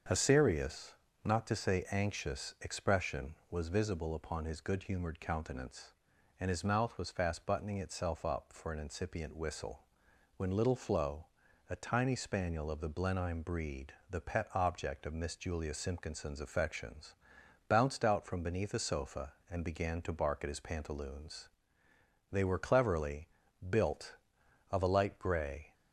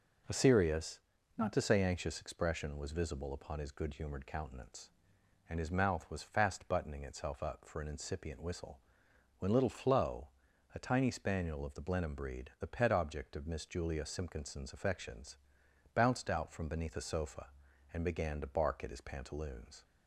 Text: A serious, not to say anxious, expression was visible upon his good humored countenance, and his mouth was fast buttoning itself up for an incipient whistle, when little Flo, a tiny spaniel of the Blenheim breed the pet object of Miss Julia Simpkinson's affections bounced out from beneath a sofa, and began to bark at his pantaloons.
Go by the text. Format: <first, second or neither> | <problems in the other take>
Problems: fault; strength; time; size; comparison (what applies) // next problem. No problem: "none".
second | starts louder than the rest; until 1.4 s; 7 dB // pauses between "breed" and "the"; slight; at 13.9 s; 0.18 s long // pauses between "affections" and "bounced"; noticeable; at 17.1 s; 0.52 s long; noticeable in the second // goes on to say "They were cleverly built of a light grey"; strong; from 22.3 s on; 3.4 s long